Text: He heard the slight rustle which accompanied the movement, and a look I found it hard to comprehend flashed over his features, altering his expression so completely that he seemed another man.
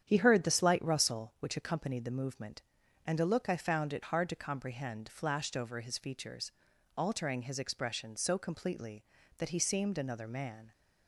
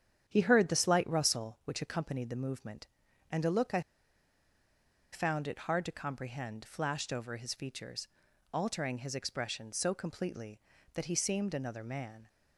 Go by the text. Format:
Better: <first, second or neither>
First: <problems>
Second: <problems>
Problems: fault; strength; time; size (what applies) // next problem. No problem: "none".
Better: first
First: starts louder than the rest; strong; until 1.0 s; 9.5 dB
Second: starts louder than the rest; strong; until 1.2 s; 9 dB // pauses between "I" and "found"; strong; at 3.8 s; 1.3 s long